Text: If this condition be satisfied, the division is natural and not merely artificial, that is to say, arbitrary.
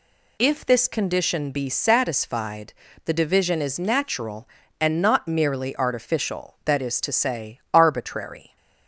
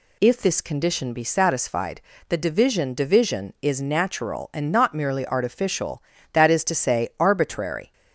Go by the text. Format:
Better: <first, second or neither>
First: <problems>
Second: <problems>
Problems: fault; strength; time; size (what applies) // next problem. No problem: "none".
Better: first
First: none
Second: says "division" twice; at 2.9 s